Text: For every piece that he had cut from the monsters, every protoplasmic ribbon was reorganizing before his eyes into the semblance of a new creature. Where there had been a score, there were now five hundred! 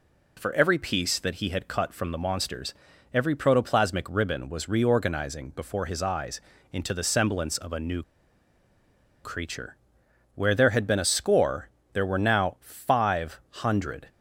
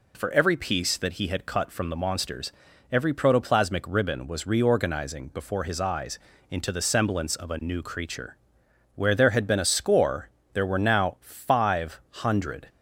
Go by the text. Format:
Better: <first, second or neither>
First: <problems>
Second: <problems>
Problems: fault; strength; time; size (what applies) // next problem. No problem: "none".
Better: second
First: pauses between "eyes" and "into"; slight; at 6.3 s; 0.32 s long // pauses between "new" and "creature"; at 8.0 s; 1.2 s long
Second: pauses between "eyes" and "into"; slight; at 6.1 s; 0.32 s long